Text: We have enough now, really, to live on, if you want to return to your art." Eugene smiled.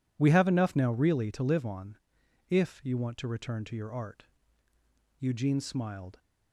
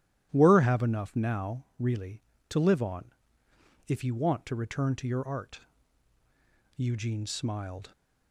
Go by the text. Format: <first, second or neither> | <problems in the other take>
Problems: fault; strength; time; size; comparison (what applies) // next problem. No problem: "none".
first | starts louder than the rest; strong; until 1.3 s; 12 dB // says "Were" for "We"; at 0.3 s